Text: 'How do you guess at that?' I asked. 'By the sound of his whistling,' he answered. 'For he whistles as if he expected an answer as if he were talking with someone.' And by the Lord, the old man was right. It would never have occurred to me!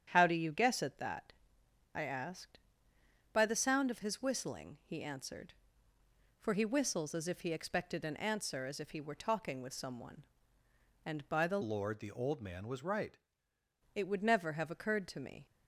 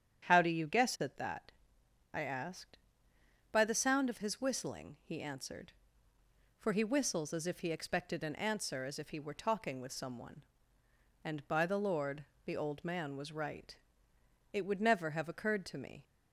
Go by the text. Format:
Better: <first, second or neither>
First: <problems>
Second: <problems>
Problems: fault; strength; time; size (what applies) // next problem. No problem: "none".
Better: second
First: starts louder than the rest; strong; until 1.1 s; 9 dB // changes voice from "Lord" to "right"; from 11.6 to 13.1 s; 1.5 s long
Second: starts louder than the rest; strong; until 1.3 s; 9 dB